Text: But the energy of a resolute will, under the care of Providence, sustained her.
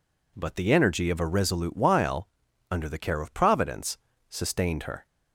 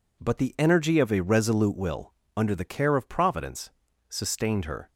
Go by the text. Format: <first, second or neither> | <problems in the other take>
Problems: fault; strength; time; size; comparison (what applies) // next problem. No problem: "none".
second | says "while" for "will"; at 1.7 s